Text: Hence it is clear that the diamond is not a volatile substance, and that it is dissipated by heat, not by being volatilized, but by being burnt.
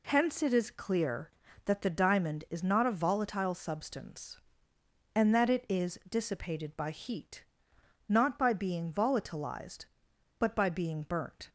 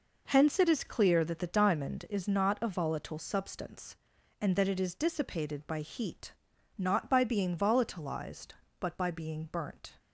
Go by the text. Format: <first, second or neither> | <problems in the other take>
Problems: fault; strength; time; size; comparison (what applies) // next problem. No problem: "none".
neither | none